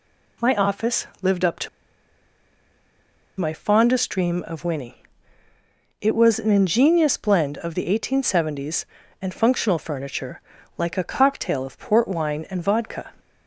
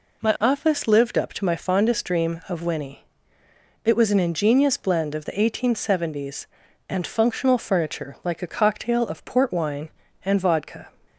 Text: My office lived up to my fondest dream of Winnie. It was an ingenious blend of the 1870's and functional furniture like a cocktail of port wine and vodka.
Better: second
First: pauses between "to" and "my"; strong; at 1.6 s; 1.7 s long // pauses between "furniture" and "like"; slight; at 10.4 s; 0.36 s long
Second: none

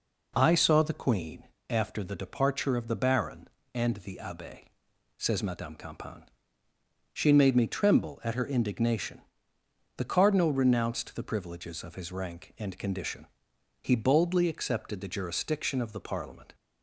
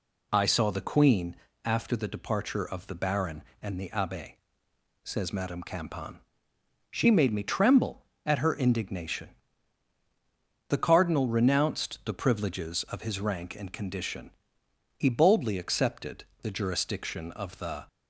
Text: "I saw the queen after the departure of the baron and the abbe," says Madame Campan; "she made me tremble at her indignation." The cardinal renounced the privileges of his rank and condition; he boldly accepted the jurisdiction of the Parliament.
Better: first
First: pauses between "queen" and "after"; slight; at 1.4 s; 0.22 s long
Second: pauses between "queen" and "after"; slight; at 1.3 s; 0.30 s long // pauses between "accepted" and "the"; slight; at 16.2 s; 0.16 s long // stops before "Parliament"; at 17.8 s

